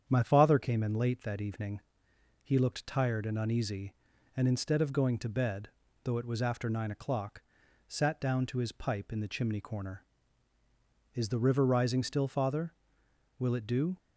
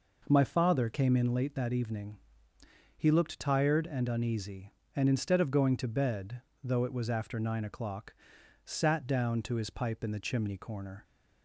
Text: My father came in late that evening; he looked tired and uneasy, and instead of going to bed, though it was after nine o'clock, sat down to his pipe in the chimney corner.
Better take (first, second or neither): second